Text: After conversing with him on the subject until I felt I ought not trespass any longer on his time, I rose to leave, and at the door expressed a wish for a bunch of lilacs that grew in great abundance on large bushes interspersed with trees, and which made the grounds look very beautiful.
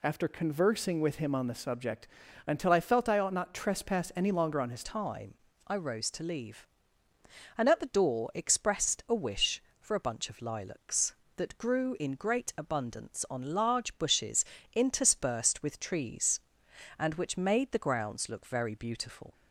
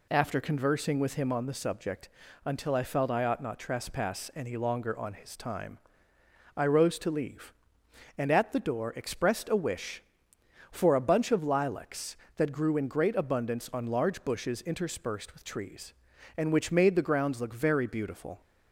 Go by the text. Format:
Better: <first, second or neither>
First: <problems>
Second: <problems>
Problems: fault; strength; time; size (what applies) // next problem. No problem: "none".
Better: second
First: pauses between "subject" and "until"; at 2.0 s; 0.40 s long // changes voice at "time"; from 4.8 s on; 14.5 s long // pauses between "bushes" and "interspersed"; slight; at 14.4 s; 0.30 s long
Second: pauses between "subject" and "until"; slight; at 2.0 s; 0.36 s long